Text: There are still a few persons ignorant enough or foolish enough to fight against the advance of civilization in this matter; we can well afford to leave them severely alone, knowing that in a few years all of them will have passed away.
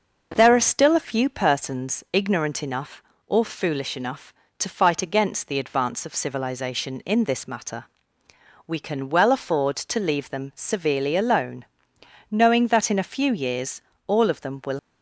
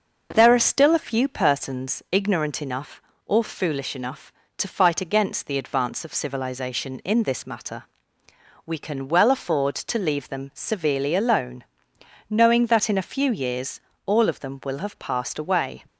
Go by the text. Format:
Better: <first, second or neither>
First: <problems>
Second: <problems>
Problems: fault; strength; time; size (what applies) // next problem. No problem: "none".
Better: second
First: pauses between "years" and "all"; slight; at 13.8 s; 0.24 s long // stops before "have passed away"; at 14.7 s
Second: pauses between "years" and "all"; slight; at 13.8 s; 0.24 s long